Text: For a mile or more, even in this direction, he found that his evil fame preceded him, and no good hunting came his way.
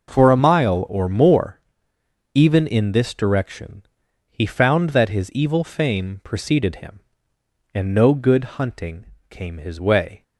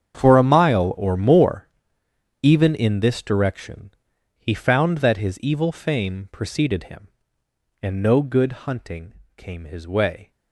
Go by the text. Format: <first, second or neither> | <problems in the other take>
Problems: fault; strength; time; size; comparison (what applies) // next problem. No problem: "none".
first | gets quieter; strong; throughout; 16.5 dB // pauses between "hunting" and "came"; slight; at 9.1 s; 0.24 s long; slight in the first